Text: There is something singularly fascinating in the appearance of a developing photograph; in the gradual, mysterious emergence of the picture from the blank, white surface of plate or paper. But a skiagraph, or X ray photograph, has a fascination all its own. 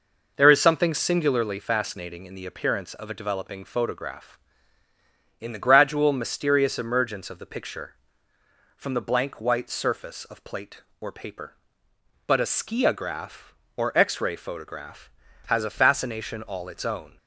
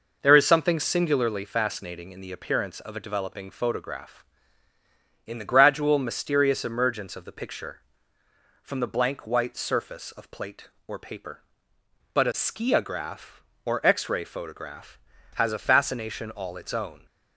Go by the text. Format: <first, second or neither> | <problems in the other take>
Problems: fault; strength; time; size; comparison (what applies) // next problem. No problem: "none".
neither | none